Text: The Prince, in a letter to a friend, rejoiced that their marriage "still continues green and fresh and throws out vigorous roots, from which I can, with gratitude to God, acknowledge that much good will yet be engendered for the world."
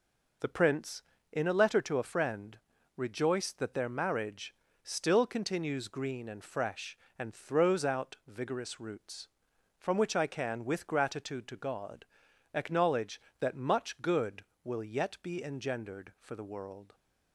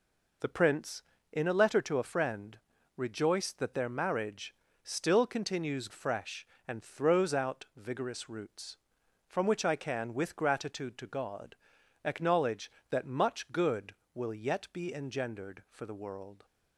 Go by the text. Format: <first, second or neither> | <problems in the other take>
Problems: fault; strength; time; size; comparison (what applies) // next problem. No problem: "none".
first | pauses between "marriage" and "still"; slight; at 4.5 s; 0.30 s long; slight in the first // skips "green and"; at 5.9 s